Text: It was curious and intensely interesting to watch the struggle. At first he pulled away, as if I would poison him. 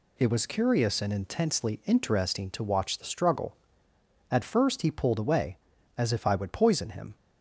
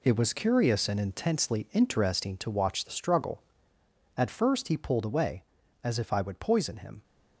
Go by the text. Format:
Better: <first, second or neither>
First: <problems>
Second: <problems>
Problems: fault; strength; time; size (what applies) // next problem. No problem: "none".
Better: first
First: none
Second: gets quieter; strong; throughout; 9 dB